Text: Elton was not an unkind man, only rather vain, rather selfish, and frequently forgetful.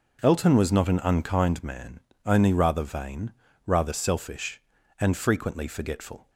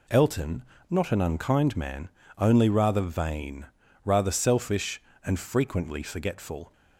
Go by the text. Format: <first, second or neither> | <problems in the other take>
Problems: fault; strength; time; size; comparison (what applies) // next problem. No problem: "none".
first | skips "was"; at 0.7 s